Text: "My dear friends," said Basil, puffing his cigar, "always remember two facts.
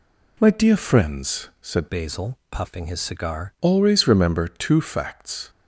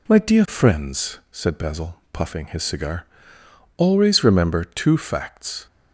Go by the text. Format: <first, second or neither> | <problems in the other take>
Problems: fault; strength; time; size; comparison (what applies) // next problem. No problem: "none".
second | changes voice from "Basil" to "cigar"; from 1.8 to 3.5 s; 1.7 s long